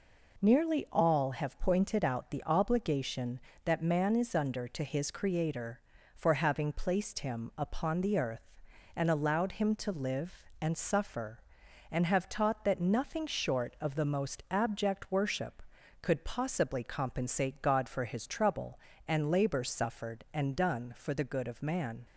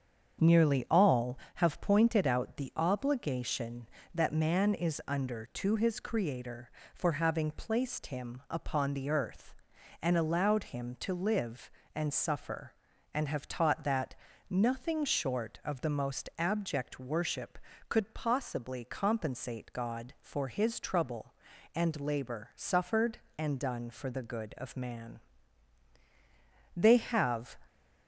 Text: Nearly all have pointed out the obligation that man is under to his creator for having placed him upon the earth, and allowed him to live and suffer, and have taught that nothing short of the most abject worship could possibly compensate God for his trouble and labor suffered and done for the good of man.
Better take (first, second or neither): first